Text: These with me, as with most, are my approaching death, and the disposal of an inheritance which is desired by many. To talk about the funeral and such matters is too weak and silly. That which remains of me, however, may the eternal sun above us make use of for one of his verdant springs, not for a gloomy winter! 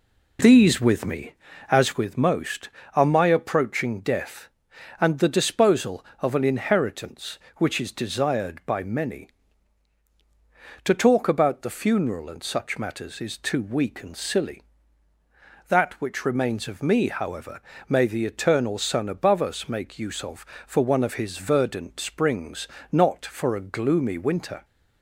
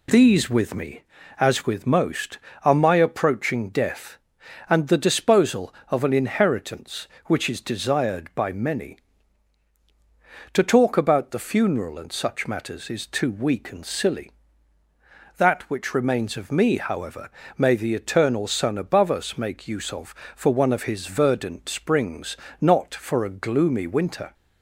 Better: second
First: starts louder than the rest; until 2.0 s; 3.5 dB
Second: none

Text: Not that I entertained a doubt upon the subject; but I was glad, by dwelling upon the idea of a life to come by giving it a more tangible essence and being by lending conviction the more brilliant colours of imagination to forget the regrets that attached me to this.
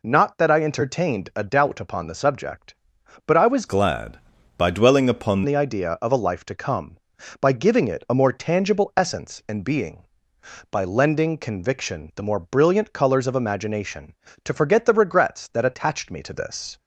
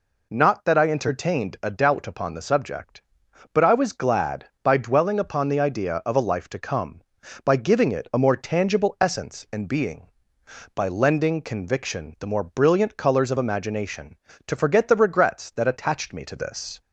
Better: second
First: changes voice from "glad" to "upon"; from 3.6 to 5.4 s; 1.8 s long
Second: none

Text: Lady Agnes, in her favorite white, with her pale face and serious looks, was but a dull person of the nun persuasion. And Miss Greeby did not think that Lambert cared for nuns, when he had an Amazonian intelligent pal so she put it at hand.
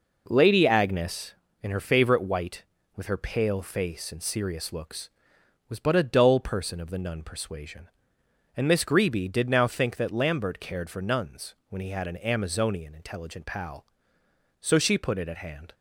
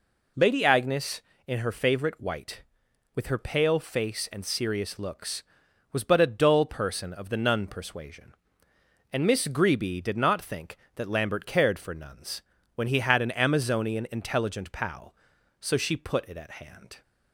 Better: second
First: says "now" for "not"; at 9.4 s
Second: none

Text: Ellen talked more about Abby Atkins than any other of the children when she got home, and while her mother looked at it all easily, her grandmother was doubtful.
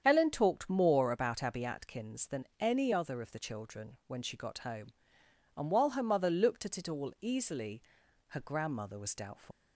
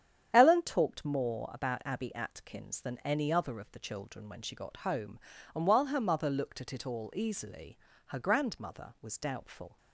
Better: second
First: starts louder than the rest; strong; until 1.0 s; 8 dB // leaves "doubtful" unfinished; at 9.5 s; 125 ms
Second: starts louder than the rest; strong; until 1.3 s; 9 dB

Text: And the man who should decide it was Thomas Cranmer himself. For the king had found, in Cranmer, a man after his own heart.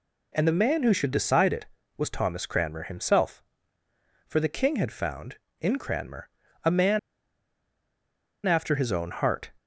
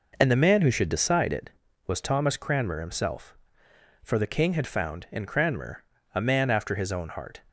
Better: second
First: pauses between "man" and "after"; strong; at 6.9 s; 1.4 s long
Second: none

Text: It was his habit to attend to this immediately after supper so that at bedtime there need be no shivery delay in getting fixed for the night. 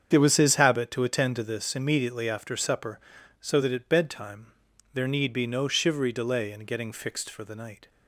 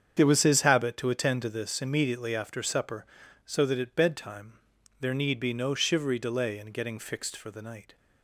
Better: neither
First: starts louder than the rest; strong; until 1.1 s; 7.5 dB // pauses between "bedtime" and "there"; at 4.4 s; 0.44 s long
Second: starts louder than the rest; strong; until 1.1 s; 7.5 dB // pauses between "bedtime" and "there"; at 4.5 s; 0.44 s long

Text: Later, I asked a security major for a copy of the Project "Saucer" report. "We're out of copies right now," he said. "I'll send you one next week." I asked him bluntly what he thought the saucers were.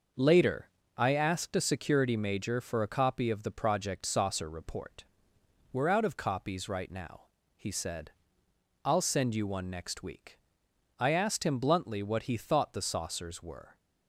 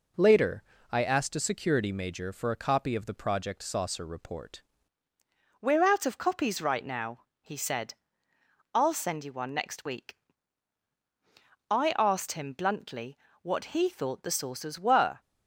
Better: first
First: none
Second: changes voice at "We're"; from 5.5 s on; 9.6 s long // pauses between "bluntly" and "what"; slight; at 13.1 s; 0.26 s long

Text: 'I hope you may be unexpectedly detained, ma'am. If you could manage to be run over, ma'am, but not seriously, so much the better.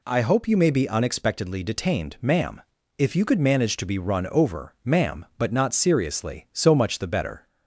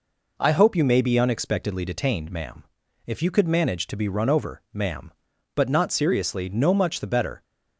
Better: first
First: none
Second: says "no" for "so"; at 6.4 s

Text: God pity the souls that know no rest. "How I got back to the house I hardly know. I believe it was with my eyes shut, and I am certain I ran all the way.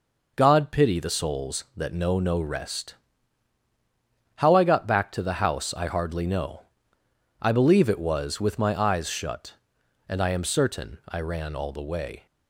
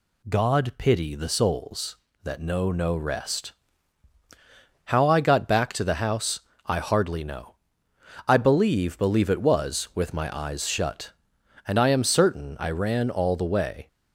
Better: first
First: none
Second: pauses between "house" and "I"; slight; at 6.3 s; 0.26 s long // says "believe" twice; at 8.9 s

